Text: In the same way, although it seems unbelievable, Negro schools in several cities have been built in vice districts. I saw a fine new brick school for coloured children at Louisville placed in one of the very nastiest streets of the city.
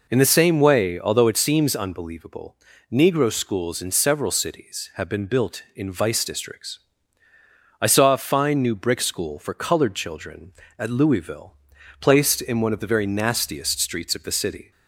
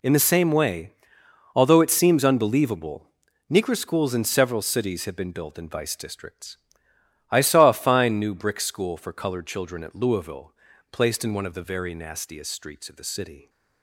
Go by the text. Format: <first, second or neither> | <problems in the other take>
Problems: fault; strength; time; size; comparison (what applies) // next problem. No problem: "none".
neither | pauses between "Louisville" and "placed"; the same in both